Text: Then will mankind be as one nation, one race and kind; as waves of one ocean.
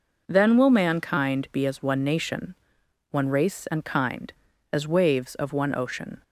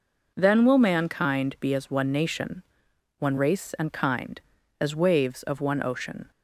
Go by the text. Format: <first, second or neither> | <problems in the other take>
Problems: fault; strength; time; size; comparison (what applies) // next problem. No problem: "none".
neither | none